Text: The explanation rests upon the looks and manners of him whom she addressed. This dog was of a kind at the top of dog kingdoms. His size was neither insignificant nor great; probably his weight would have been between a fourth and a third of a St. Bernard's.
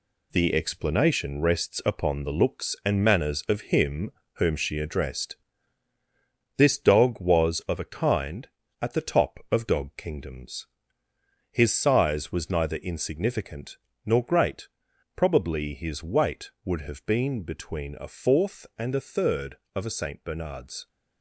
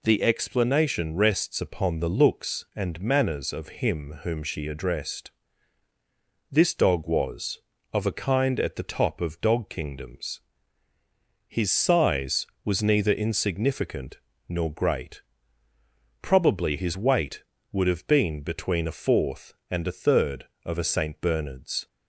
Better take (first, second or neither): second